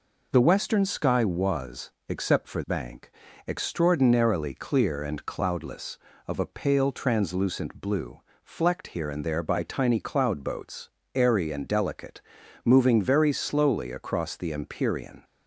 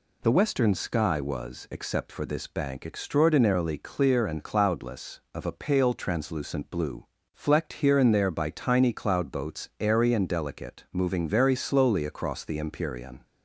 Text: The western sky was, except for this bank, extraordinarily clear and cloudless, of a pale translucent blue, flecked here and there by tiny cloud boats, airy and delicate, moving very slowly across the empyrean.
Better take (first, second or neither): second